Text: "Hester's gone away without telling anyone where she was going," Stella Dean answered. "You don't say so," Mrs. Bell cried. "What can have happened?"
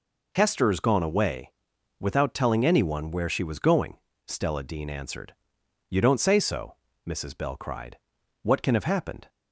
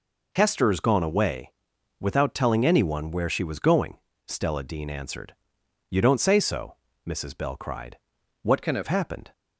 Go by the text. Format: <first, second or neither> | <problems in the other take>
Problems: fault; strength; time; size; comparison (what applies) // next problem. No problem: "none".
first | pauses between "away" and "without"; noticeable; at 1.5 s; 0.48 s long; noticeable in the first // changes voice from "can" to "have"; from 8.6 to 8.8 s; 0.2 s long